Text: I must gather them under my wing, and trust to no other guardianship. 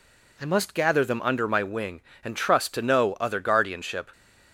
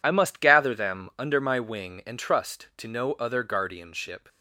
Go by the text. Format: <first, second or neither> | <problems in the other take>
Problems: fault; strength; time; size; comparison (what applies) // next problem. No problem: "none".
neither | none